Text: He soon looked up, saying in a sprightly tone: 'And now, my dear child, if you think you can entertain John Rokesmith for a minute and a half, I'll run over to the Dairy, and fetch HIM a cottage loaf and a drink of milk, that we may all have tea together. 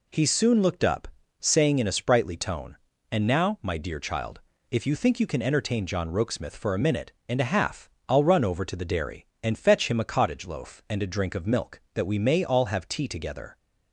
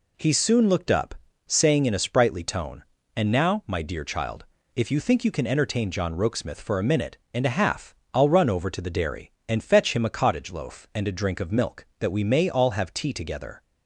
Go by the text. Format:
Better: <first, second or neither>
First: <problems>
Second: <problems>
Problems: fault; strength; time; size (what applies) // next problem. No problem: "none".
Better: neither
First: none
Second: none